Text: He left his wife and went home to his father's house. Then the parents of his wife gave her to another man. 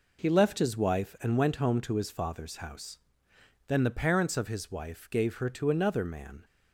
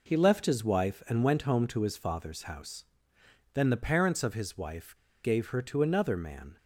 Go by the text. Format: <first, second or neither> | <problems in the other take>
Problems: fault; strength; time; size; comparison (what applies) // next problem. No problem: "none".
first | pauses between "wife" and "gave"; slight; at 4.9 s; 0.28 s long